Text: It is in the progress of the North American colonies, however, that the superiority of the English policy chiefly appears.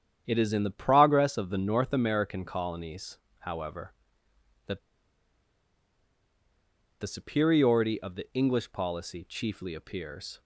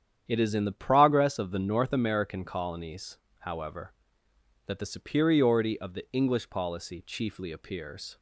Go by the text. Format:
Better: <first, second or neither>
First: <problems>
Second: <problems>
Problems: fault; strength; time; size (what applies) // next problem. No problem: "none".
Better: second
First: starts louder than the rest; strong; until 1.2 s; 9 dB // pauses between "that" and "the"; strong; at 4.7 s; 2.2 s long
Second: starts louder than the rest; strong; until 1.2 s; 9 dB